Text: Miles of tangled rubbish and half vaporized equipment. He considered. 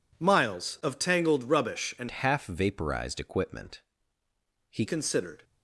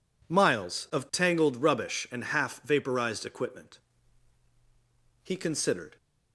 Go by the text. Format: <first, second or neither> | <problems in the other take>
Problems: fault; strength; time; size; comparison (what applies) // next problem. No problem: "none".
second | changes voice from "half" to "He"; from 2.1 to 4.8 s; 2.7 s long